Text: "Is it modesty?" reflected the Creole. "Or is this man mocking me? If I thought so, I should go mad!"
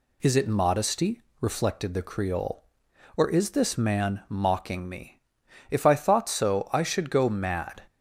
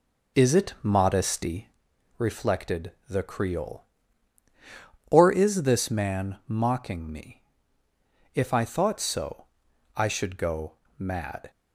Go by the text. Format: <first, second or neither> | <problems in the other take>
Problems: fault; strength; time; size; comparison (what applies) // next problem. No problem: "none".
first | starts louder than the rest; noticeable; until 1.8 s; 5 dB // pauses between "reflected" and "the"; slight; at 2.9 s; 0.16 s long // pauses between "go" and "mad"; slight; at 10.7 s; 0.24 s long